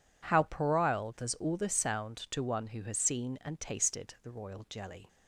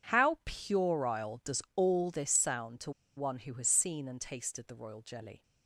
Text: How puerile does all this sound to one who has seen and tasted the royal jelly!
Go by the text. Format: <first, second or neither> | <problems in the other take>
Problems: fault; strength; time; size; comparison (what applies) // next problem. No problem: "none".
first | pauses between "to" and "one"; slight; at 2.9 s; 0.26 s long